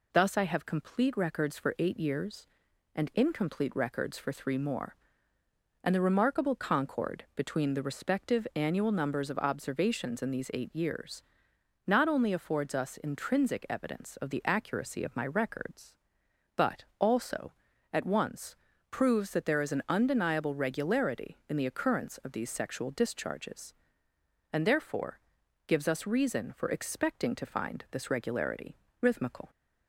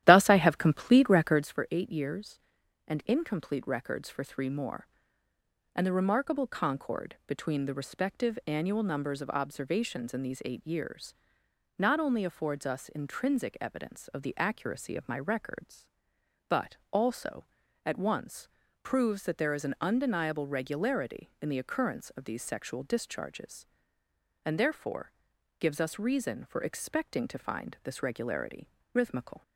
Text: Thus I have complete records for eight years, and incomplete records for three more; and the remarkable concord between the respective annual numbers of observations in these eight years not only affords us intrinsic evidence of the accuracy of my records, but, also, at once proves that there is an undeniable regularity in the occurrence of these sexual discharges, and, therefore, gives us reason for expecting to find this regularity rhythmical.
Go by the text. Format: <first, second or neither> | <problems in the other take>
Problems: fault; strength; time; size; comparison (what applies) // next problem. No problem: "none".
first | starts louder than the rest; strong; until 1.5 s; 12.5 dB // pauses between "years" and "not"; noticeable; at 11.1 s; 0.64 s long; noticeable in the first // pauses between "once" and "proves"; slight; at 18.4 s; 0.34 s long; slight in the first // pauses between "regularity" and "rhythmical"; slight; at 28.6 s; 0.28 s long; slight in the first